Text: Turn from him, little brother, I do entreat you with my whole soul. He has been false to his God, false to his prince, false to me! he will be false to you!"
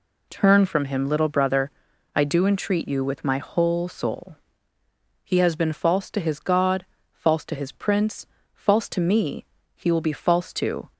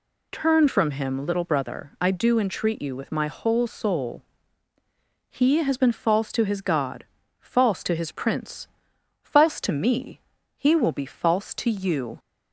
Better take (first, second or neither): second